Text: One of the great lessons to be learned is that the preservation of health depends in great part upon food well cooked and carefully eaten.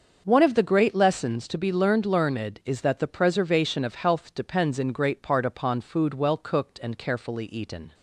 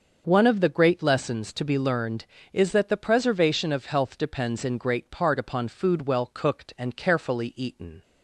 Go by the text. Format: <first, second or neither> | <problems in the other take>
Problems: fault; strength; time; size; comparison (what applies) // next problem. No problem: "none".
second | starts louder than the rest; until 1.2 s; 6.5 dB; also in the second // says "learned" twice; at 2.0 s